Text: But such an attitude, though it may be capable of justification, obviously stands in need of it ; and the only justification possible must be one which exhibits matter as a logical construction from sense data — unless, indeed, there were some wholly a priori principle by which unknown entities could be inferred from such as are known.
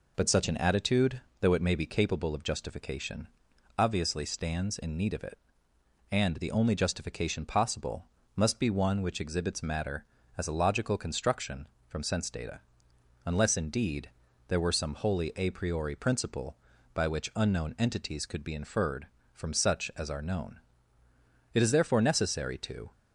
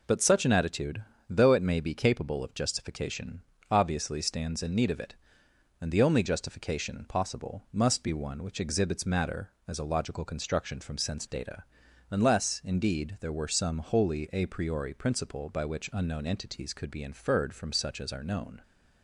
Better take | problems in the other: second | pauses between "possible" and "must"; slight; at 8.0 s; 0.30 s long // goes on to say "It is therefore necessary to"; from 21.5 s on; 1.4 s long

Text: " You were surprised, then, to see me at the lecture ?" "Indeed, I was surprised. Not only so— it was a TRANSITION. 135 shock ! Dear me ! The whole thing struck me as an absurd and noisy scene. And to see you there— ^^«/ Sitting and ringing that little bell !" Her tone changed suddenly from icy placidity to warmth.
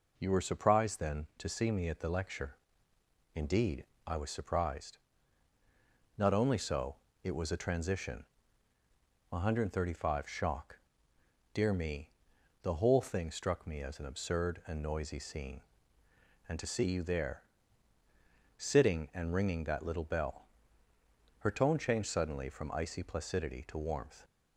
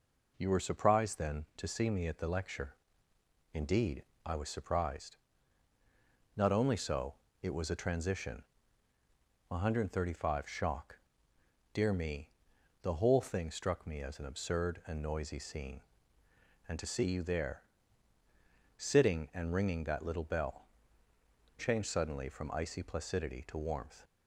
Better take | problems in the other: first | skips "Her tone"; at 21.5 s

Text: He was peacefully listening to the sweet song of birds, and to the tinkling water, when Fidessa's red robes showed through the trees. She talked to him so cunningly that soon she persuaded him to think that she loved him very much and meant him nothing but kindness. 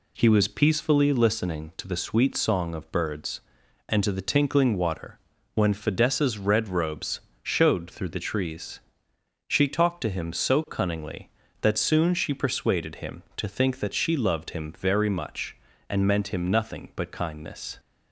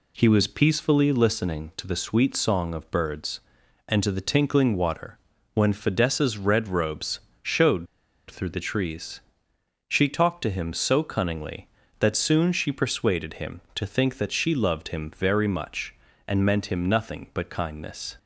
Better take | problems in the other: first | pauses between "robes" and "showed"; slight; at 7.1 s; 0.22 s long; slight in the first // pauses between "showed" and "through"; at 7.8 s; 0.44 s long

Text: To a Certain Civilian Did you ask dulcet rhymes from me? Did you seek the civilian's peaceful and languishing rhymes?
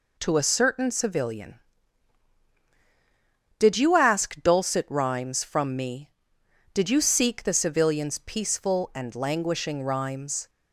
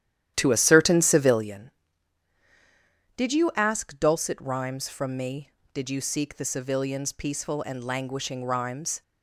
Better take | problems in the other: first | starts louder than the rest; strong; until 1.6 s; 11.5 dB

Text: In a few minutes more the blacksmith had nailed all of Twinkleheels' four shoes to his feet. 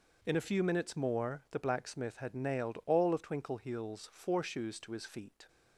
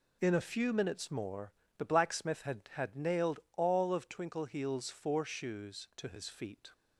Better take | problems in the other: first | pauses between "more" and "the"; slight; at 1.5 s; 0.24 s long // says "had" twice; at 2.7 s // pauses between "nailed" and "all"; slight; at 3.3 s; 0.16 s long

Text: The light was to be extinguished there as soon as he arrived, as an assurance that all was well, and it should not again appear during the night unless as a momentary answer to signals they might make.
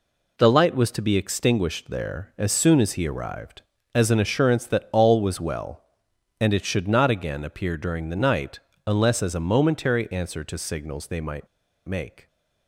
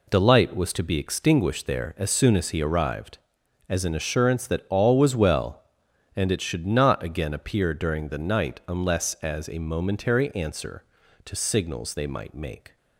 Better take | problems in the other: second | pauses between "night" and "unless"; slight; at 8.6 s; 0.26 s long // pauses between "might" and "make"; at 11.4 s; 0.39 s long

